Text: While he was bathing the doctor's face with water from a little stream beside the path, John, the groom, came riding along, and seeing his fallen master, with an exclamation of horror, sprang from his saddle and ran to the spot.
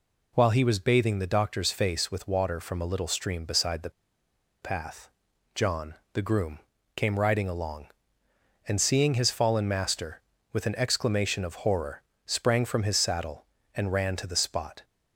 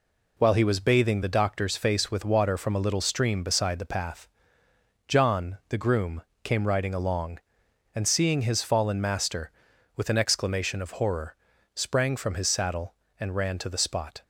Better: second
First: pauses between "the" and "path"; noticeable; at 3.9 s; 0.72 s long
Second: none

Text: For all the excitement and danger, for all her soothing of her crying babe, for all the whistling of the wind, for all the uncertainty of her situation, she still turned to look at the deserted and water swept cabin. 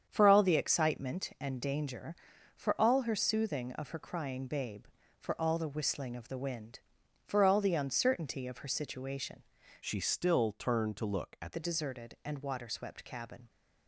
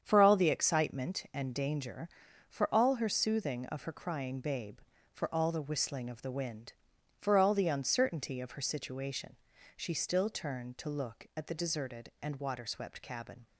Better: second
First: starts louder than the rest; strong; until 1.0 s; 8 dB // changes voice from "she" to "at"; from 9.8 to 11.5 s; 1.7 s long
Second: starts louder than the rest; strong; until 1.0 s; 8 dB

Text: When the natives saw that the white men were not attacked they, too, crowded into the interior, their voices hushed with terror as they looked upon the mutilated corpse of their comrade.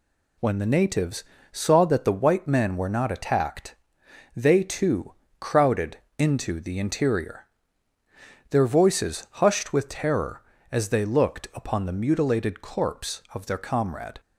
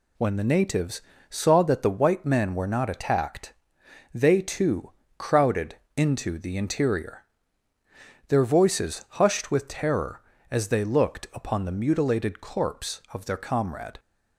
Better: neither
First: pauses between "natives" and "saw"; slight; at 1.2 s; 0.28 s long // pauses between "attacked" and "they"; noticeable; at 3.7 s; 0.64 s long // pauses between "crowded" and "into"; slight; at 5.9 s; 0.22 s long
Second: pauses between "natives" and "saw"; slight; at 1.0 s; 0.28 s long // pauses between "attacked" and "they"; noticeable; at 3.5 s; 0.64 s long // pauses between "crowded" and "into"; slight; at 5.7 s; 0.22 s long

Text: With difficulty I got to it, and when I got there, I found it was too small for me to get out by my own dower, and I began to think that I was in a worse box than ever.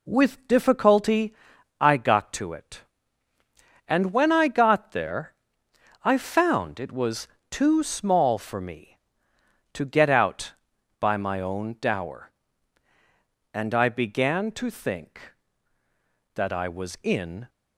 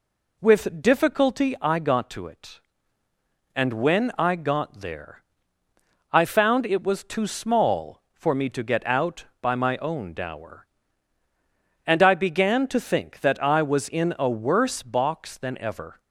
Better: second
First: pauses between "difficulty" and "I"; noticeable; at 1.3 s; 0.46 s long // pauses between "was" and "too"; slight; at 7.2 s; 0.24 s long // stops before "a worse box than ever"; at 17.4 s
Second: none

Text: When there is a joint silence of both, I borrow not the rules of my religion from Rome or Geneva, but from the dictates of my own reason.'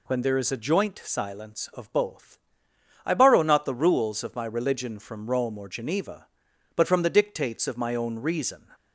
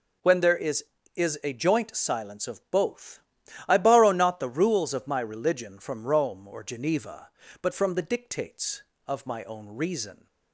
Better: first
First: none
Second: says "is" twice; at 1.1 s

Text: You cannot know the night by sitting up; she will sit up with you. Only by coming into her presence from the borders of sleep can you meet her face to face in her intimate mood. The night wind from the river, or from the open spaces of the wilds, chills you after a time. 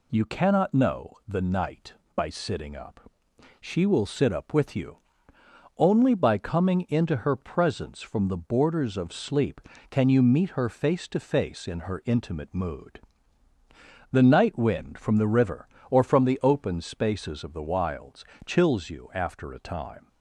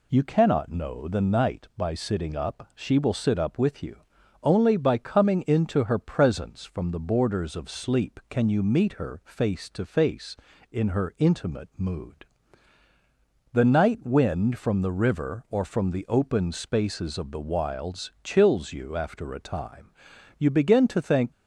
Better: first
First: none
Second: goes on to say "You begin to think"; noticeable; from 20.4 s on; 0.90 s long

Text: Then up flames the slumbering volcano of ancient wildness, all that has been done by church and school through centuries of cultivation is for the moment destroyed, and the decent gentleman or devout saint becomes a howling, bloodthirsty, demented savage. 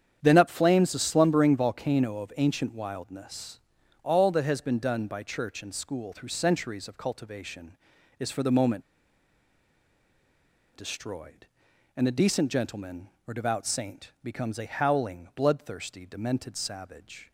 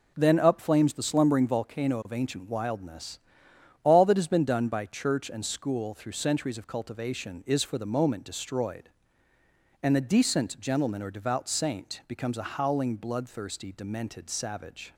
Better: second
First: starts louder than the rest; strong; until 1.2 s; 8.5 dB // pauses between "moment" and "destroyed"; strong; at 8.8 s; 1.9 s long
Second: none

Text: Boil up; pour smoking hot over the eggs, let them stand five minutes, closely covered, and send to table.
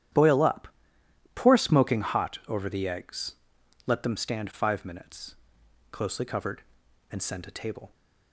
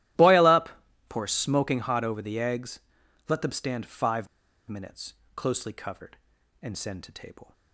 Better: first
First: starts louder than the rest; strong; until 1.7 s; 11 dB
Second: starts louder than the rest; strong; until 1.5 s; 15 dB // pauses between "five" and "minutes"; at 4.2 s; 0.43 s long

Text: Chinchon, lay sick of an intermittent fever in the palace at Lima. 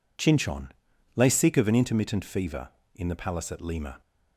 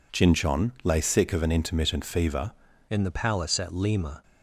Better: first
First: none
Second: changes voice at "in"; from 2.9 s on; 1.3 s long

